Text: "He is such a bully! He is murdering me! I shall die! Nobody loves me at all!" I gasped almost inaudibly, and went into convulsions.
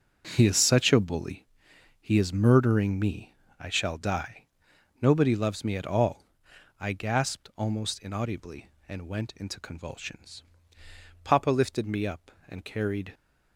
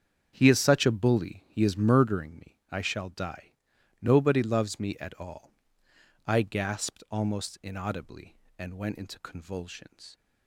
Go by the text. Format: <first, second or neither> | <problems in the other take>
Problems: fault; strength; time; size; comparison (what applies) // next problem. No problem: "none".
second | starts louder than the rest; strong; until 1.3 s; 7.5 dB; strong in the second // goes on to say "Papa lifted me up and carried"; strong; from 11.2 s on; 1.9 s long